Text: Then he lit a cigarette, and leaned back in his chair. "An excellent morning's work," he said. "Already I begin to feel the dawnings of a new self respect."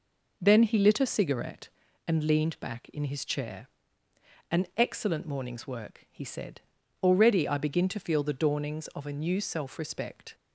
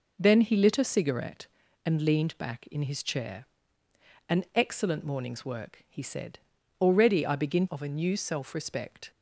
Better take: first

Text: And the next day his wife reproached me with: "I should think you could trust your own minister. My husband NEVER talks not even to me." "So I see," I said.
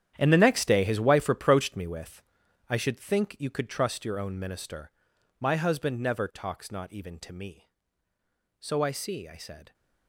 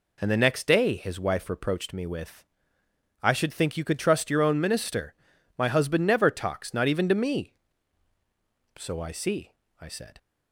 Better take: second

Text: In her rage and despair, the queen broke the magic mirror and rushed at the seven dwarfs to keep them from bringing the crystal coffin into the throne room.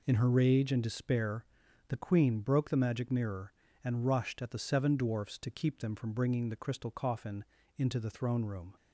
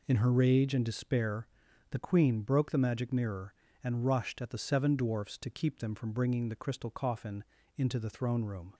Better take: neither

